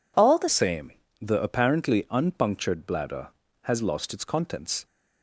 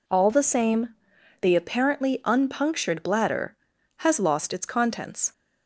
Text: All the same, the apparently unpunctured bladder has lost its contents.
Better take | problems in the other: second | changes voice at "same"; from 0.4 s on; 4.4 s long

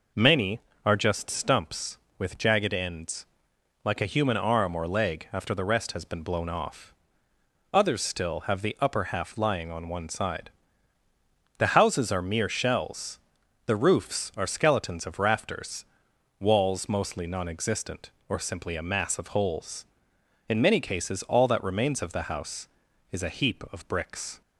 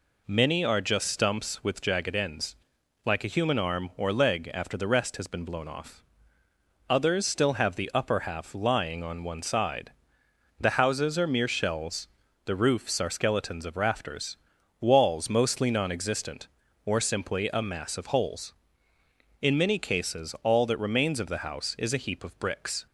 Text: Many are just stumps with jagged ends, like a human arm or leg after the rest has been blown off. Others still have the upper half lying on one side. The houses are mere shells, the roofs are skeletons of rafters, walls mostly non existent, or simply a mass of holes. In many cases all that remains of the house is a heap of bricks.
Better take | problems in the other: neither | none

